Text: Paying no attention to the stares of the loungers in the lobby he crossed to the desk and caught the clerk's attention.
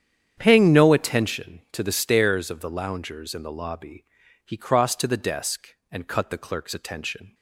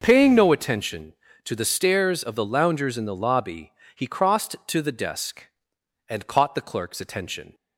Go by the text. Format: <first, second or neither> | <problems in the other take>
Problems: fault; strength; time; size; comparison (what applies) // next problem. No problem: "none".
second | starts louder than the rest; strong; until 1.3 s; 9 dB // pauses between "lobby" and "he"; at 4.0 s; 0.40 s long; slight in the second // says "cut" for "caught"; at 6.0 s